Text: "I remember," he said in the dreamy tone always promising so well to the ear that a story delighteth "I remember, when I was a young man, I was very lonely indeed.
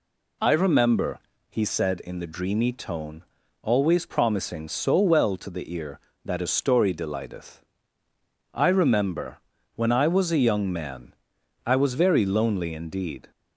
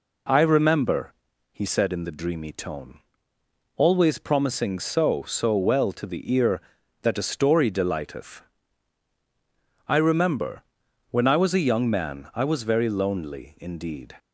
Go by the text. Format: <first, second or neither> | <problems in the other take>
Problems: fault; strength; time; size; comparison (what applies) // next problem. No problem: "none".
first | pauses between "tone" and "always"; noticeable; at 2.9 s; 0.78 s long; also in the first // says "so" twice; at 5.2 s // pauses between "delighteth" and "I"; strong; at 8.4 s; 1.4 s long; noticeable in the first